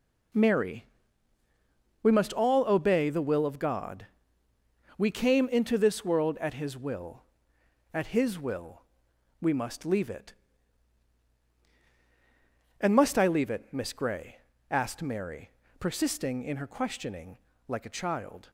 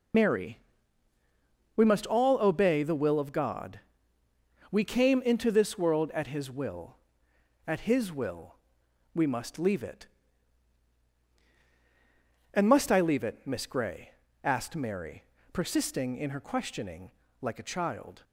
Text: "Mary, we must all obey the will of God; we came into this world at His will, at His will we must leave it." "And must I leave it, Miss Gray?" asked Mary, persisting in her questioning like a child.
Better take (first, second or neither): first